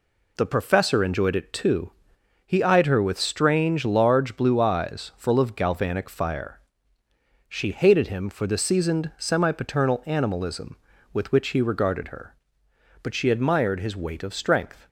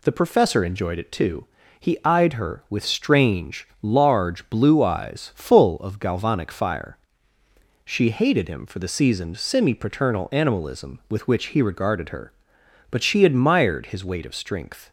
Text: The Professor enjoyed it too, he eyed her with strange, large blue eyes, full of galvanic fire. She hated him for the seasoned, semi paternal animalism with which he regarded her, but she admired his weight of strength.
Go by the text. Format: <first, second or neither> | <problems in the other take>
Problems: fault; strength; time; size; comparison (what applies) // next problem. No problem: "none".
neither | none